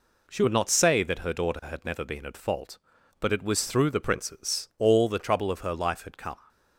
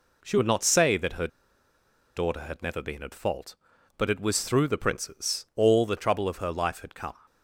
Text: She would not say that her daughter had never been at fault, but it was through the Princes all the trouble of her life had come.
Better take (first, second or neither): first